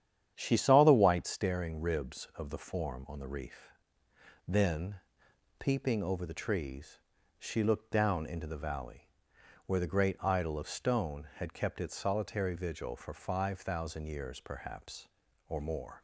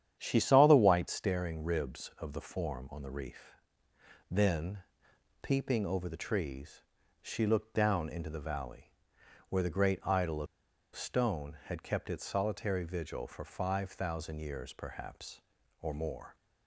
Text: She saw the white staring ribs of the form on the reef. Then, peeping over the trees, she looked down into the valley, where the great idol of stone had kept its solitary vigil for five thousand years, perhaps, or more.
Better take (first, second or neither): first